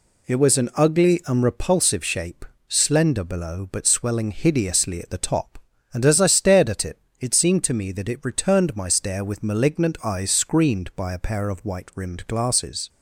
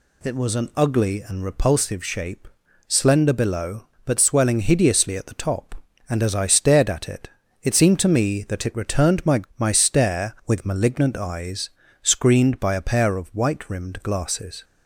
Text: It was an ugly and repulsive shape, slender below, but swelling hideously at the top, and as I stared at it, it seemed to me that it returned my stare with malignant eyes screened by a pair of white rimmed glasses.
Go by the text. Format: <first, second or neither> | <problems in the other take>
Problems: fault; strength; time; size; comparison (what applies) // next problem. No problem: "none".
first | says "my" twice; at 9.5 s // pauses between "eyes" and "screened"; slight; at 11.6 s; 0.34 s long